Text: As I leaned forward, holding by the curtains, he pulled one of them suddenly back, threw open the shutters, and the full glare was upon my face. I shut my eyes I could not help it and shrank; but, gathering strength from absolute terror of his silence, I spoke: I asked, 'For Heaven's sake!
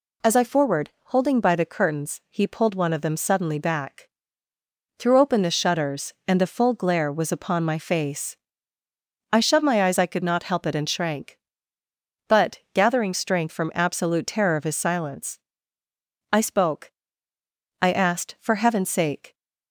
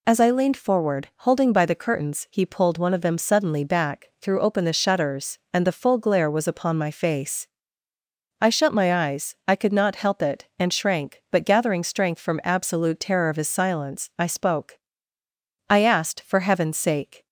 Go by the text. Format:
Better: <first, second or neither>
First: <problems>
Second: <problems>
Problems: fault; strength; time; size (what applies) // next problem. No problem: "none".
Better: second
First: skips "leaned"; at 0.4 s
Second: none